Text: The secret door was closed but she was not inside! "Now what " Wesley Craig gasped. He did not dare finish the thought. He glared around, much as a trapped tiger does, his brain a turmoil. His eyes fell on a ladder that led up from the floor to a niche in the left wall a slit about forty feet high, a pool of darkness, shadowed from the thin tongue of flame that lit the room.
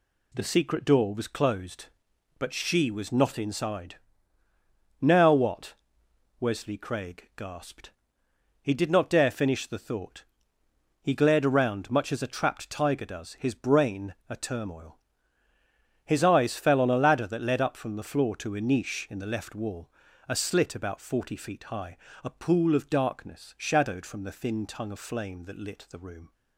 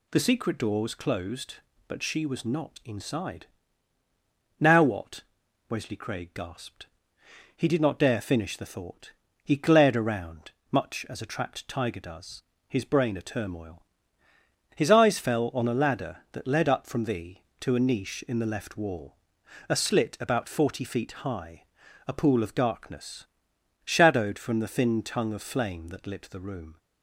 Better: first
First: pauses between "wall" and "a"; at 19.8 s; 0.38 s long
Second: skips "floor"; at 17.4 s // pauses between "wall" and "a"; noticeable; at 19.1 s; 0.52 s long

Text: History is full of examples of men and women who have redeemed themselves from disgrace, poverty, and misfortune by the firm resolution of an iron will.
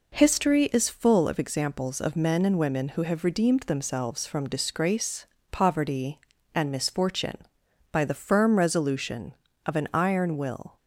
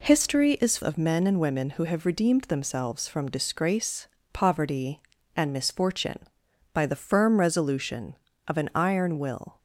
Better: first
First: none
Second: skips "full of examples"; at 0.8 s

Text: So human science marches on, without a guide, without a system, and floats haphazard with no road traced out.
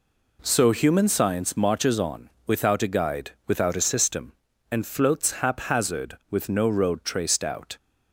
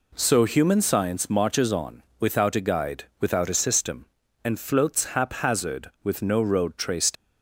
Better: first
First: none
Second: stops before "out"; at 7.1 s

